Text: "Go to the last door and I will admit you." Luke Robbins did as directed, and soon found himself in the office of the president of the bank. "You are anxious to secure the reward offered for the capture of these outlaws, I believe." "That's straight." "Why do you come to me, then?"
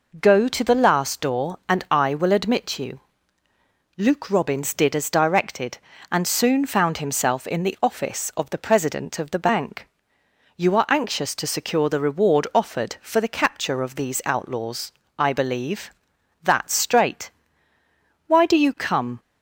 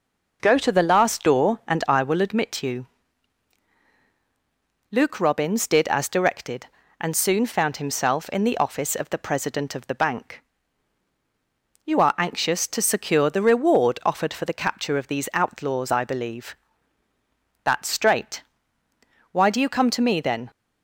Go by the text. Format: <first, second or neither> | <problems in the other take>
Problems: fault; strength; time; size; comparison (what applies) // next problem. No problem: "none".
second | stops before "to me then"; at 19.1 s